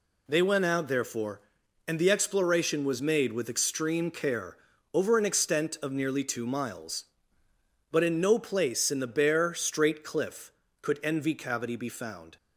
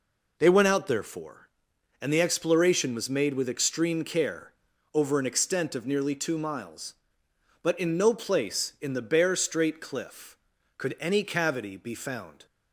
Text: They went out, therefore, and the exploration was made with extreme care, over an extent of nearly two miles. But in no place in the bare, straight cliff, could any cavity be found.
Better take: second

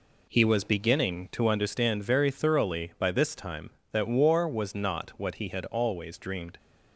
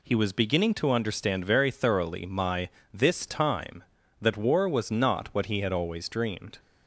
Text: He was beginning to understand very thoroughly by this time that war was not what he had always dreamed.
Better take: first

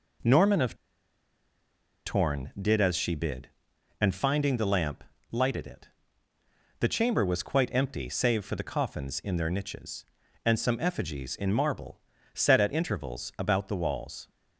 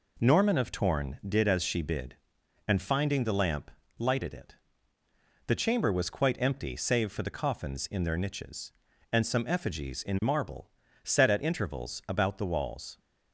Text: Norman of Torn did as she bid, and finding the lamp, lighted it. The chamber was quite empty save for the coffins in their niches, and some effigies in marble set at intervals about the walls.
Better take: second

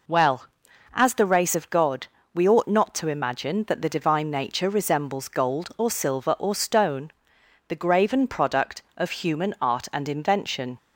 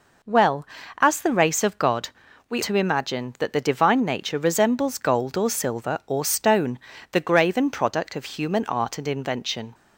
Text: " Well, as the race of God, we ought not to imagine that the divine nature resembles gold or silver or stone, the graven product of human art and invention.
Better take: first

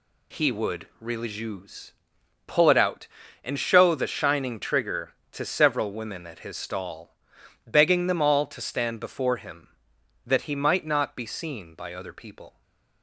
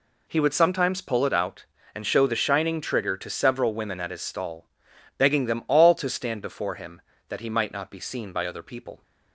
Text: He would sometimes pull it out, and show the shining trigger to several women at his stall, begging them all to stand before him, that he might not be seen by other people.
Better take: second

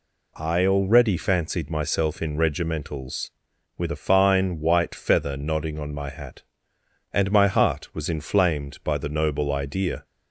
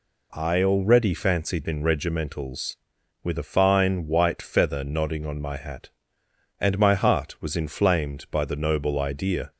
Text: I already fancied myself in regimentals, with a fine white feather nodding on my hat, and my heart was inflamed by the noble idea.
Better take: first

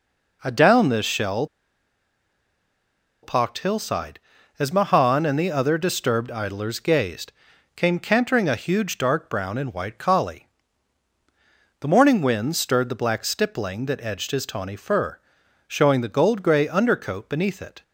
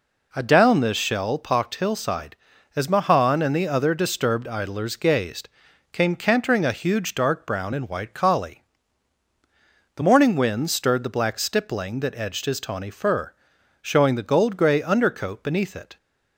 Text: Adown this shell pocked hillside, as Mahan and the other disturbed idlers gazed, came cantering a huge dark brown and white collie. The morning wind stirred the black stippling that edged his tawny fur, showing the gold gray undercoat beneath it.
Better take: second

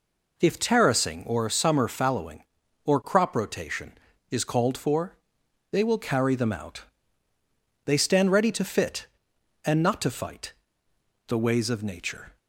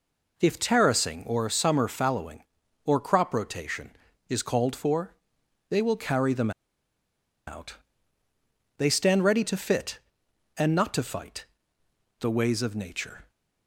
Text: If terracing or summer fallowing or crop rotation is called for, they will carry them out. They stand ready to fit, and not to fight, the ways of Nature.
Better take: first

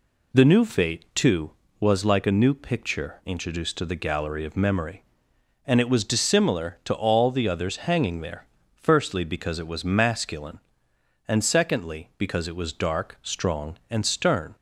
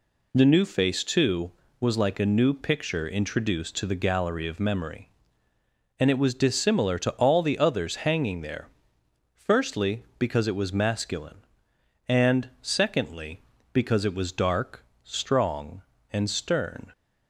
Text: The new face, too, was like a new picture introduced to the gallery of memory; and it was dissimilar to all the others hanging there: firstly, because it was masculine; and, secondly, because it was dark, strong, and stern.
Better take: second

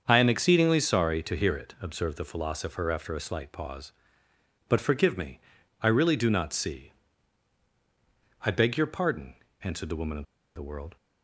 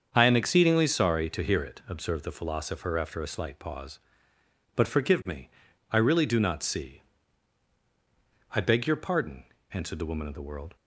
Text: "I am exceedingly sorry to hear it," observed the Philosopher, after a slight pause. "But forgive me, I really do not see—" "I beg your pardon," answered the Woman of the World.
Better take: second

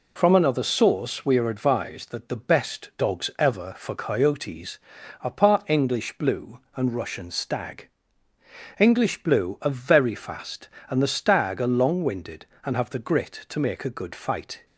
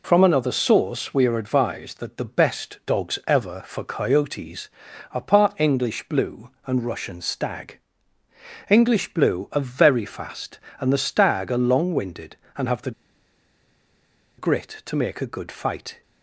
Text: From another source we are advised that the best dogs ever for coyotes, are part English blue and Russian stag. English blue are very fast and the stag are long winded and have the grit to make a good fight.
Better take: first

